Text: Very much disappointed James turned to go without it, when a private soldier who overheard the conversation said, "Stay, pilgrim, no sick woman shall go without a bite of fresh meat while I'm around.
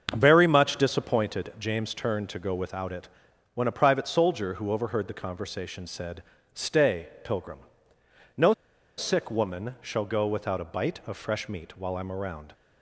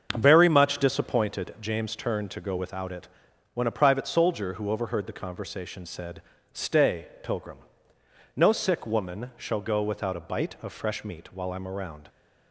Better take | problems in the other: second | starts louder than the rest; until 1.1 s; 7 dB; also in the second // pauses between "no" and "sick"; noticeable; at 8.5 s; 0.46 s long

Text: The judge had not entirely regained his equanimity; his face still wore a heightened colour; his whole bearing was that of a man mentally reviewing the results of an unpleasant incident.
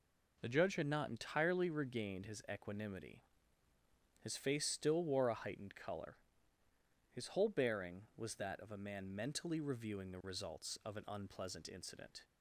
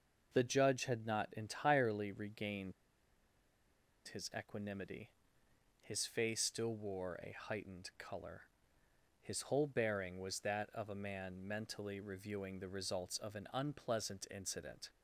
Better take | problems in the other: first | pauses between "regained" and "his"; strong; at 2.7 s; 1.3 s long

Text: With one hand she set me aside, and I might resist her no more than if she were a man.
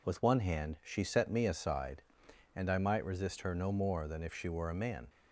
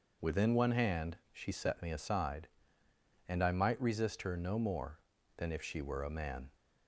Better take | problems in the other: first | says "Within" for "With"; at 0.2 s // pauses between "hand" and "she"; slight; at 1.1 s; 0.16 s long

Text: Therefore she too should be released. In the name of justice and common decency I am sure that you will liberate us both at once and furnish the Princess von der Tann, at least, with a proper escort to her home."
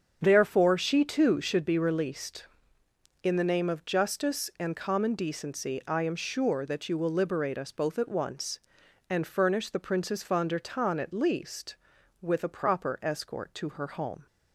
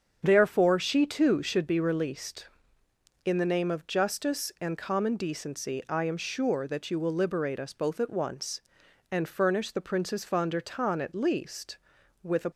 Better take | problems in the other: first | starts louder than the rest; strong; until 1.2 s; 7.5 dB; strong in the first // stops before "proper escort to her home"; at 12.5 s

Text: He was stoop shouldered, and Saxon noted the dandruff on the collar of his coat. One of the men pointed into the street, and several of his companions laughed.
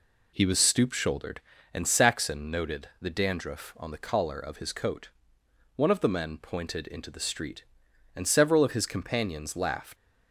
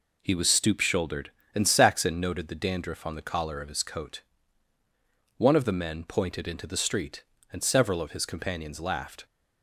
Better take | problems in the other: second | leaves "laughed" unfinished; at 9.9 s; 85 ms

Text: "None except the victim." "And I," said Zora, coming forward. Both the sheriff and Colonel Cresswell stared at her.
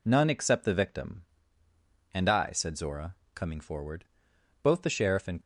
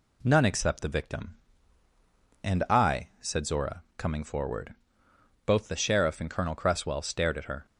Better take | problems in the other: second | stops before "Colonel Cresswell stared at her"; at 5.4 s

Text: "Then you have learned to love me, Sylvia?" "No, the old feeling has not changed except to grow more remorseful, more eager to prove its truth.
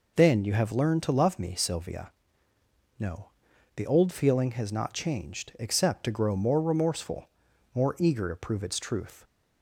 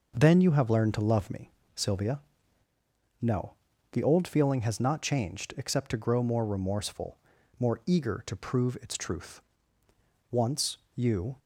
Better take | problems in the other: first | goes on to say "Once you"; noticeable; from 10.3 s on; 1.0 s long

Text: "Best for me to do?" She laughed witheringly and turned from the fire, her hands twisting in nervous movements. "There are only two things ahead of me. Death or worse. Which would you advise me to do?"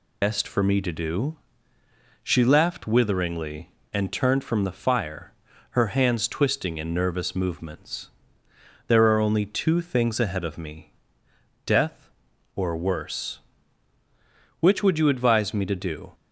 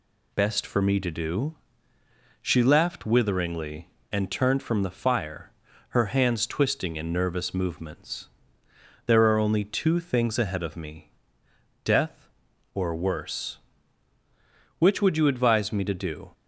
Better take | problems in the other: second | loses the start of "Best"; at 0.2 s; 70 ms

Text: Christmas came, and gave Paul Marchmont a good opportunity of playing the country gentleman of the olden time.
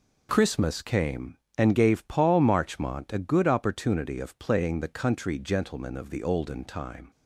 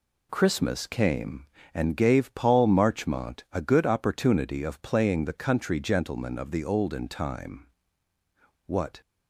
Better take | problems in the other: first | goes on to say "What"; slight; from 8.6 s on; 0.34 s long

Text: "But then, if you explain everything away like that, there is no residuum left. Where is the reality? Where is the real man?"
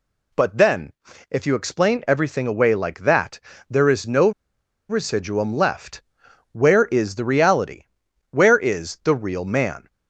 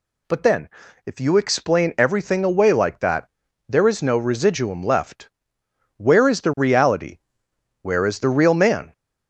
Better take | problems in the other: second | pauses between "no" and "residuum"; noticeable; at 4.3 s; 0.58 s long

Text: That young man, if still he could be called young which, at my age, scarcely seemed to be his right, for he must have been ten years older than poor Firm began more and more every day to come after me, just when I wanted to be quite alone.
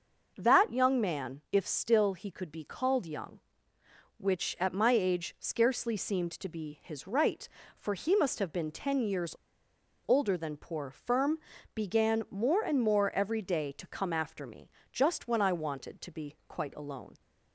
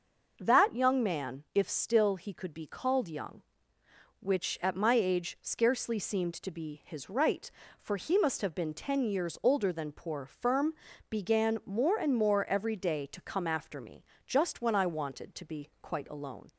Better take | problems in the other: second | starts louder than the rest; noticeable; until 1.3 s; 6 dB // pauses between "years" and "older"; noticeable; at 9.3 s; 0.73 s long // pauses between "Firm" and "began"; at 11.3 s; 0.38 s long; also in the second

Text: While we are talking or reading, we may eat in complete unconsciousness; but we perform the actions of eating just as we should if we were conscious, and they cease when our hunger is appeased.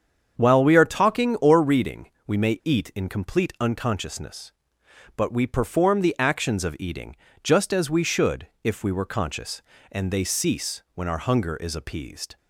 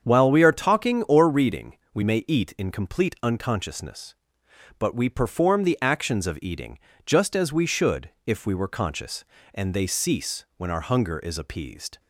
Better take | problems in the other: neither | starts louder than the rest; strong; the same in both // pauses between "eating" and "just"; slight; the same in both // pauses between "should" and "if"; slight; the same in both

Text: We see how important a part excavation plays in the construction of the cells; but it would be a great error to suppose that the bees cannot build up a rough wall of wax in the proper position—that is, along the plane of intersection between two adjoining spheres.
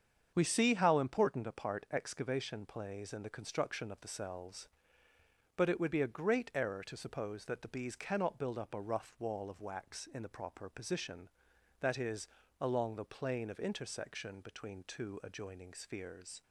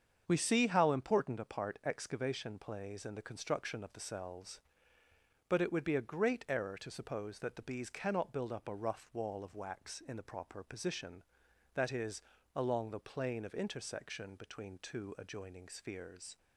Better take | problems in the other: neither | starts louder than the rest; strong; the same in both

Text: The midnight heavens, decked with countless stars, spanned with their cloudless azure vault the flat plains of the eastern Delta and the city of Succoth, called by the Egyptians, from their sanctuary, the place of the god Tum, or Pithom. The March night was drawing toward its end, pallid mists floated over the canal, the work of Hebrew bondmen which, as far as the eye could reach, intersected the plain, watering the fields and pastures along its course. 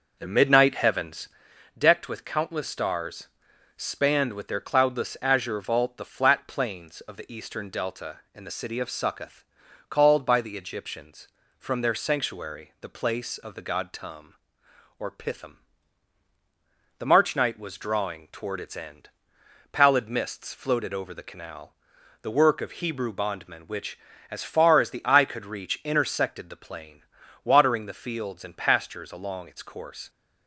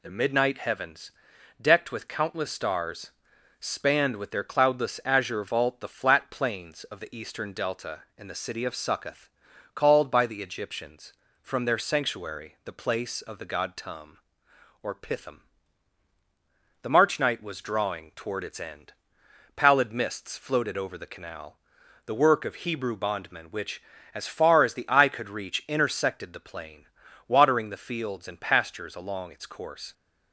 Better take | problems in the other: second | starts louder than the rest; noticeable; until 1.5 s; 6 dB

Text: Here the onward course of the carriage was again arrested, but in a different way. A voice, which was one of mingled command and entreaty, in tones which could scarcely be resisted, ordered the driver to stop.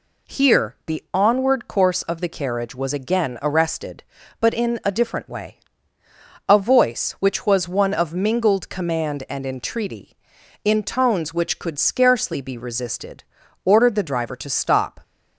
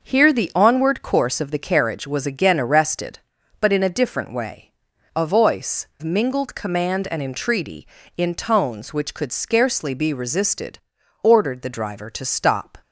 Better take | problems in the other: first | starts louder than the rest; noticeable; until 1.0 s; 6 dB // skips "which was one of"; at 5.9 s

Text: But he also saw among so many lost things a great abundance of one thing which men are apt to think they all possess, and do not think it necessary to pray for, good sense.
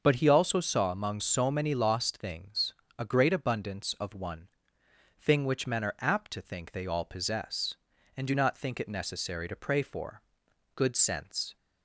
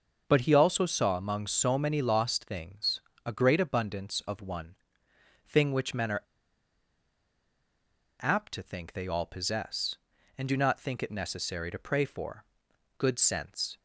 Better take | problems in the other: first | starts louder than the rest; until 1.2 s; 6 dB; also in the first // pauses between "things" and "a"; slight; at 2.9 s; 0.24 s long; slight in the first // pauses between "one" and "thing"; noticeable; at 4.7 s; 0.72 s long; noticeable in the first // pauses between "are" and "apt"; strong; at 6.2 s; 1.9 s long

